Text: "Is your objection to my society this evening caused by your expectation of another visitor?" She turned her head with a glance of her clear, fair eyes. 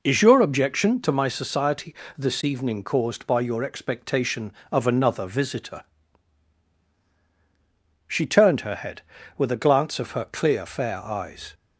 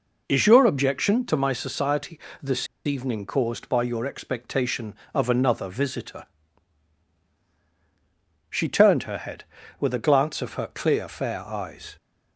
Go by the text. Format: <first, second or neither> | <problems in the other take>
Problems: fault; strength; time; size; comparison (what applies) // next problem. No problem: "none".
first | pauses between "society" and "this"; slight; at 2.1 s; 0.24 s long; slight in the first // pauses between "this" and "evening"; slight; at 2.6 s; 0.19 s long